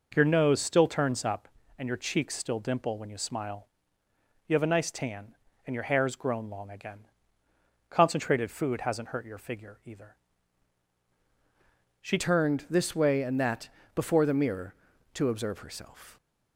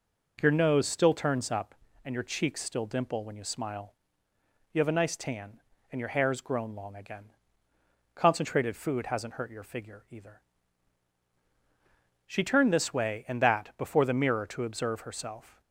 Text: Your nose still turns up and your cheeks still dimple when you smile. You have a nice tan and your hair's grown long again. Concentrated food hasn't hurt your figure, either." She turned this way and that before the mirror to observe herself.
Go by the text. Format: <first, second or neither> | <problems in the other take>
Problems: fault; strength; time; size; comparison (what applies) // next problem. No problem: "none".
second | changes voice at "turned"; from 12.1 s on; 4.0 s long // pauses between "that" and "before"; slight; at 13.6 s; 0.26 s long